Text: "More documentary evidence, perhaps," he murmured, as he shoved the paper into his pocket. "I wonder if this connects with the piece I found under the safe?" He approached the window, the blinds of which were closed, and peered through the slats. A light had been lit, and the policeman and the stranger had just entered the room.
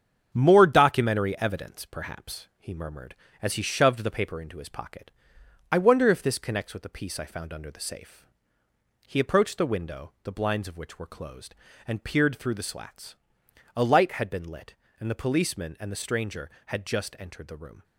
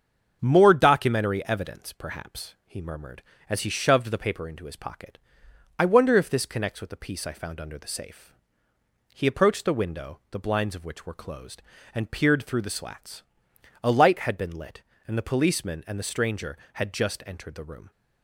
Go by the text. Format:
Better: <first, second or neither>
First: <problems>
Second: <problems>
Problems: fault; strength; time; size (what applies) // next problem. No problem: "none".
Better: second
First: gets quieter; noticeable; throughout; 5 dB // starts louder than the rest; strong; until 1.3 s; 8 dB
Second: starts louder than the rest; strong; until 1.4 s; 7 dB